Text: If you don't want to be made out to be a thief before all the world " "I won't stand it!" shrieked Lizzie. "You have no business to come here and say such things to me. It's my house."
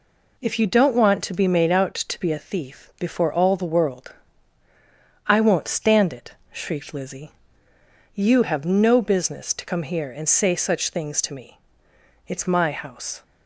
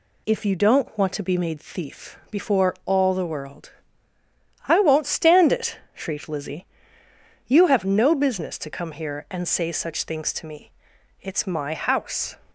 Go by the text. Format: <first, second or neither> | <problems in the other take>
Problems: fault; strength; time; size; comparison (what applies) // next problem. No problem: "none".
first | skips "out to be a"; at 1.5 s